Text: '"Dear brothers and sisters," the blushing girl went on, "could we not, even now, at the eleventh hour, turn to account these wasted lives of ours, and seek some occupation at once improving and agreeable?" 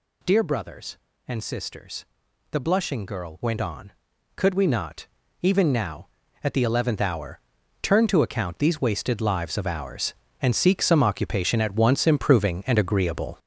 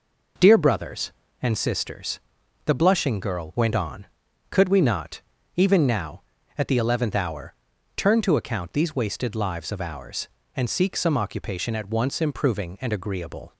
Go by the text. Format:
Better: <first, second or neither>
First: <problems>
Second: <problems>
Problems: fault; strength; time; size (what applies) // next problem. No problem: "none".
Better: second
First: gets louder; throughout; 6.5 dB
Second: none